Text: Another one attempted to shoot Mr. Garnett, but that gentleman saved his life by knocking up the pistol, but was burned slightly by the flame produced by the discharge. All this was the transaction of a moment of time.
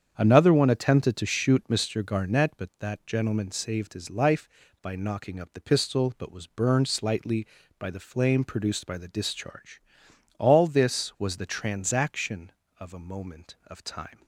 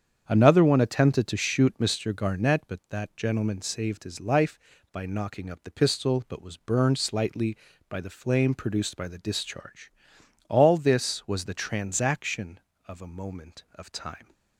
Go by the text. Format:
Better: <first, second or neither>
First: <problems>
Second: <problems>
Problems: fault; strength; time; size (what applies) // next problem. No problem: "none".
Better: neither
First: starts louder than the rest; strong; until 1.1 s; 8 dB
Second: starts louder than the rest; strong; until 1.2 s; 8 dB